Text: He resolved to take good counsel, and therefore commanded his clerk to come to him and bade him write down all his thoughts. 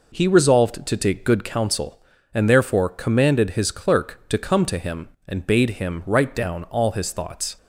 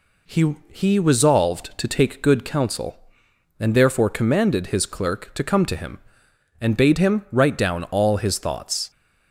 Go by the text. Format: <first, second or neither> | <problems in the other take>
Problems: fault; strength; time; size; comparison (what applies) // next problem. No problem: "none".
first | says "He" twice; at 0.6 s